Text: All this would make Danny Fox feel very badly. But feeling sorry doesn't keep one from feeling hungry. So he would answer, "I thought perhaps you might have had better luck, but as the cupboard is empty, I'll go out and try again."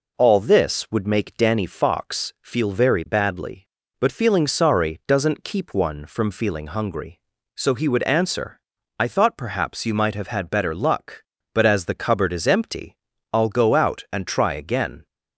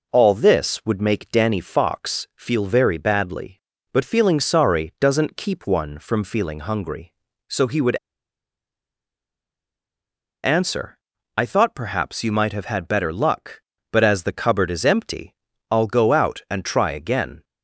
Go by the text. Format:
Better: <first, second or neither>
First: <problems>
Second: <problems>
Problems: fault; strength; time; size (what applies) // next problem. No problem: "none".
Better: first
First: none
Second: pauses between "would" and "answer"; strong; at 7.9 s; 2.4 s long